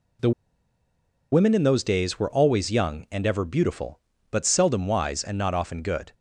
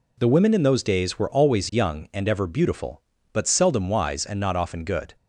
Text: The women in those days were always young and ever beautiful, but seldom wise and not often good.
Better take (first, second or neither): second